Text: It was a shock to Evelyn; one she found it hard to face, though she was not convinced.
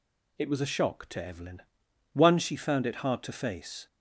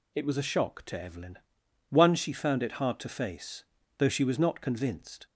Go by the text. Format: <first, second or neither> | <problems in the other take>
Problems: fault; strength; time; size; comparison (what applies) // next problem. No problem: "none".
second | stops before "though she was not convinced"; at 3.8 s